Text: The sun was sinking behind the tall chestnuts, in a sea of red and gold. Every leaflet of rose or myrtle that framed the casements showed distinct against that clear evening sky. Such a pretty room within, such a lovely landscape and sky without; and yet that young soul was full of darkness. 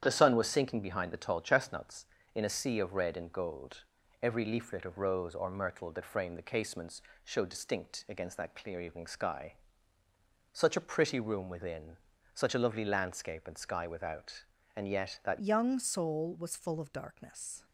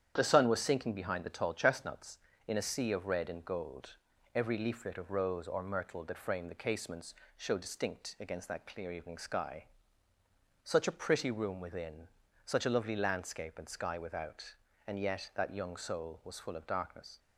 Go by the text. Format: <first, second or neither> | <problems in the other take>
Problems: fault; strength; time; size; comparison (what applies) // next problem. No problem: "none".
second | starts louder than the rest; strong; until 1.0 s; 9.5 dB; strong in the second // pauses between "casements" and "showed"; slight; at 6.9 s; 0.24 s long; slight in the second // changes voice at "young"; from 15.3 s on; 2.3 s long